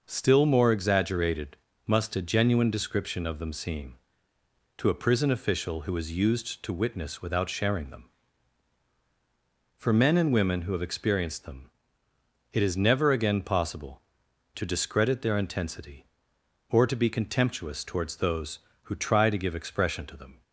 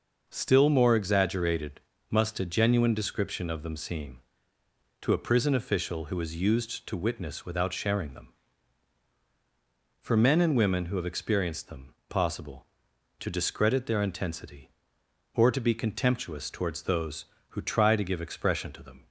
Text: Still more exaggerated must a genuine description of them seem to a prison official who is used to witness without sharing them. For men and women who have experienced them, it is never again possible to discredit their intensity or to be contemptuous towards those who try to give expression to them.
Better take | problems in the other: first | pauses between "exaggerated" and "must"; slight; at 1.7 s; 0.30 s long; slight in the first // skips "it is never again"; at 12.0 s

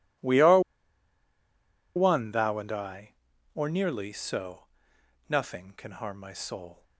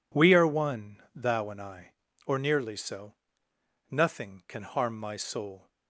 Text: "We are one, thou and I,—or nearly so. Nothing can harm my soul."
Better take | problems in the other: second | pauses between "are" and "one"; strong; at 0.5 s; 1.3 s long

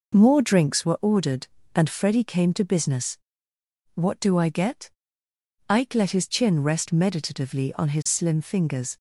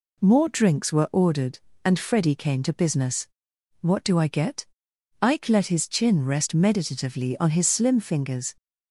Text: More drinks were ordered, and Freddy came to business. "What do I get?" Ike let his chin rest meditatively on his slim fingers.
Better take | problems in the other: neither | none

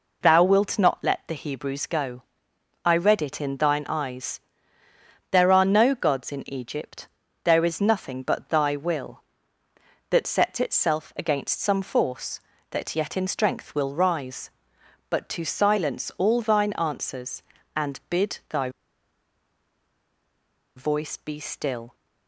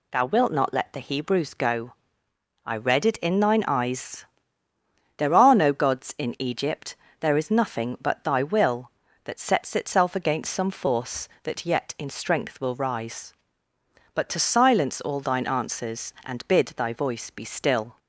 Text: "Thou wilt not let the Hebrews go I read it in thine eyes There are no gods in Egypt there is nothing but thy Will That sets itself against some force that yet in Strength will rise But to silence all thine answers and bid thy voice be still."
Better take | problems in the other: second | pauses between "go" and "I"; noticeable; at 2.2 s; 0.62 s long; noticeable in the second // pauses between "eyes" and "There"; noticeable; at 4.3 s; 0.94 s long; noticeable in the second // pauses between "Egypt" and "there"; slight; at 7.0 s; 0.34 s long; slight in the second // pauses between "thy" and "voice"; strong; at 18.7 s; 2.0 s long

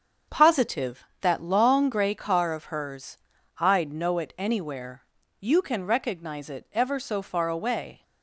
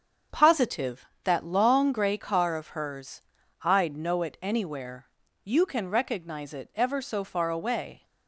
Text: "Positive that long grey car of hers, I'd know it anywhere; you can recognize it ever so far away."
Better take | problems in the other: neither | starts louder than the rest; the same in both

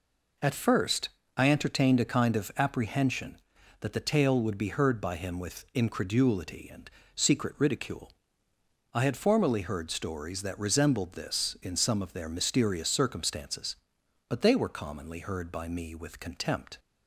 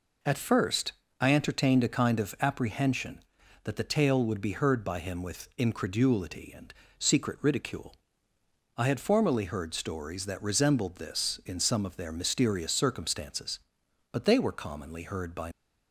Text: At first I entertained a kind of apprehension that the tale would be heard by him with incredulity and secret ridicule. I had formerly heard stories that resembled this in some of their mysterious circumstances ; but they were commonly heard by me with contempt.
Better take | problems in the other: first | pauses between "first" and "I"; slight; at 0.9 s; 0.28 s long; slight in the first // pauses between "and" and "secret"; slight; at 6.7 s; 0.26 s long; slight in the first // stops before "me with contempt"; at 15.5 s

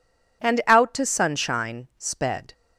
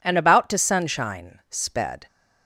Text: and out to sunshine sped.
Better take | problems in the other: first | says "about" for "out"; at 0.1 s

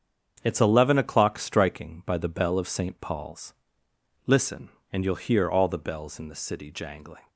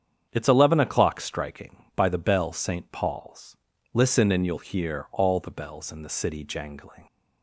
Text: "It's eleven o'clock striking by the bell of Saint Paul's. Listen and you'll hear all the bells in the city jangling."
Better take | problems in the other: first | starts louder than the rest; strong; until 1.3 s; 8 dB; strong in the first // skips "of"; at 2.5 s

